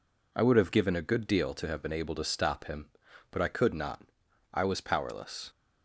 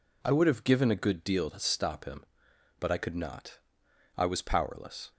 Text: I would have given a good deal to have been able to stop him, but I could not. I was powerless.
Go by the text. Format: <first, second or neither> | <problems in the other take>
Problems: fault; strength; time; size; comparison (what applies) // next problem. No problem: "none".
first | skips "to have been able"; at 1.4 s